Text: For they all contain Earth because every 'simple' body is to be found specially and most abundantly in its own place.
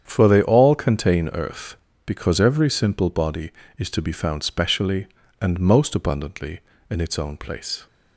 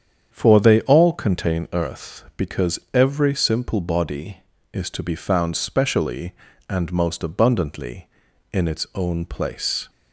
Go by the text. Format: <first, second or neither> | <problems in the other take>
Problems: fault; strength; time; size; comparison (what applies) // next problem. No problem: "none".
neither | starts louder than the rest; strong; the same in both